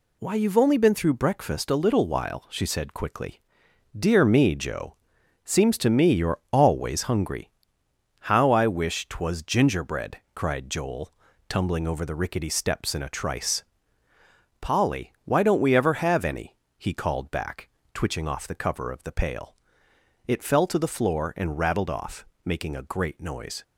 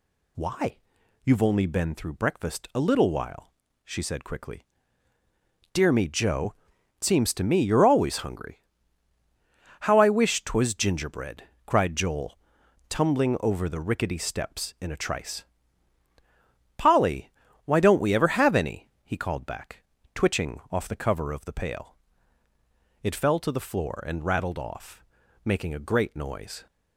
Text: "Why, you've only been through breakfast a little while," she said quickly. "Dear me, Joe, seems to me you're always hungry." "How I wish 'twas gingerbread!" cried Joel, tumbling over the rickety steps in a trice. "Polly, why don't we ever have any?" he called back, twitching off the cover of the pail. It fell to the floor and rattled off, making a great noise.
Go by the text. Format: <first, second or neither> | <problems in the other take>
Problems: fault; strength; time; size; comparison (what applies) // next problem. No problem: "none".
neither | none